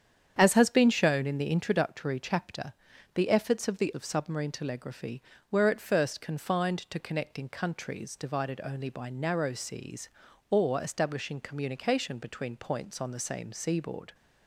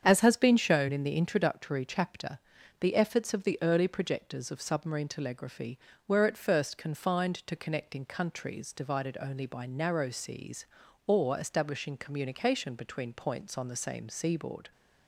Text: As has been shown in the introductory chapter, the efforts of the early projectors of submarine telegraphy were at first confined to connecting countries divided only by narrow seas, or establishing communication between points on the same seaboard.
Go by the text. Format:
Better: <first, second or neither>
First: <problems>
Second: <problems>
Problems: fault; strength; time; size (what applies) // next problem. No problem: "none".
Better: second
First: starts louder than the rest; strong; until 1.3 s; 8.5 dB // skips "early projectors"; at 3.9 s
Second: starts louder than the rest; strong; until 1.0 s; 8 dB